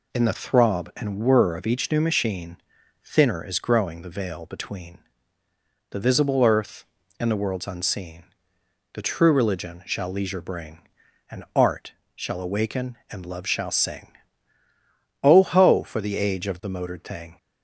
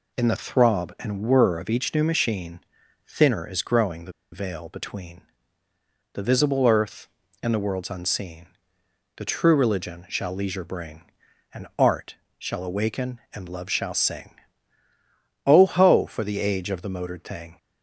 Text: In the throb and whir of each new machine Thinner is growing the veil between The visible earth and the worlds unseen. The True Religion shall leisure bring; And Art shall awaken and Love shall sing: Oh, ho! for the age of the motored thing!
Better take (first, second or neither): first